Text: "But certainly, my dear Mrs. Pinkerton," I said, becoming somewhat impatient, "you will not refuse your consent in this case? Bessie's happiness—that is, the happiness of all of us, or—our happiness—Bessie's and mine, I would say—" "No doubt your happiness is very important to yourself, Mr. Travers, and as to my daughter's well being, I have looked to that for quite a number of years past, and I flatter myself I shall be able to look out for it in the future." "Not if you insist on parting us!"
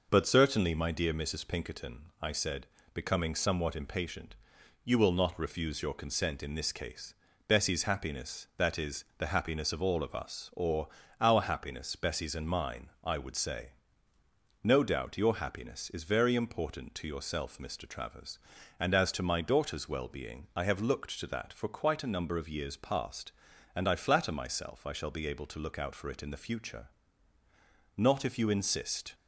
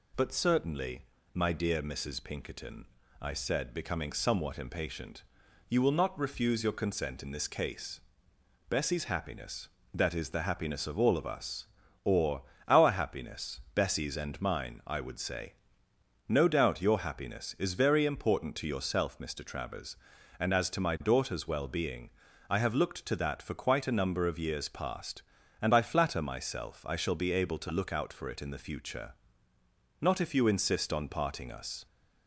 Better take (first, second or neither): second